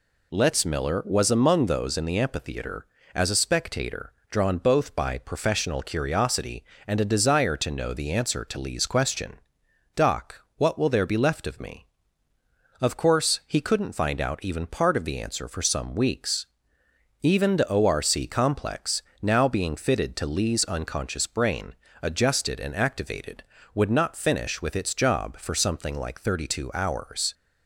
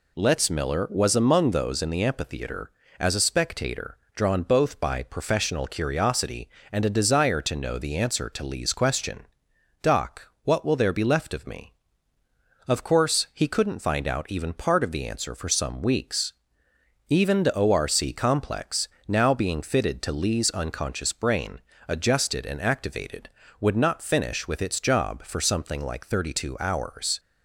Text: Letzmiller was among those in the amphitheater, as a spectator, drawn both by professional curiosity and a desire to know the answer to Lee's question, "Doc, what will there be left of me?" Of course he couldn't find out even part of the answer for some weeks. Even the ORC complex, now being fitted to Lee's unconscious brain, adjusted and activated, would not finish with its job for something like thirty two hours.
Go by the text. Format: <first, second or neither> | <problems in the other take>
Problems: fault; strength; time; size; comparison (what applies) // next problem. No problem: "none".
neither | none